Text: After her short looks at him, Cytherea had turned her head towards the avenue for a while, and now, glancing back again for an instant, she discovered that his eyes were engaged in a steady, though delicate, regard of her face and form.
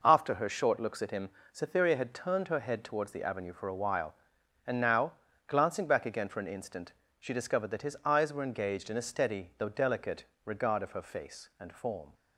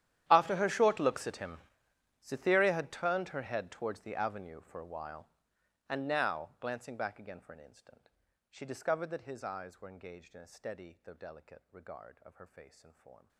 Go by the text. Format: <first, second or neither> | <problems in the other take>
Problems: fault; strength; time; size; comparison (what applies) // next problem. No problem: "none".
first | gets quieter; strong; throughout; 24 dB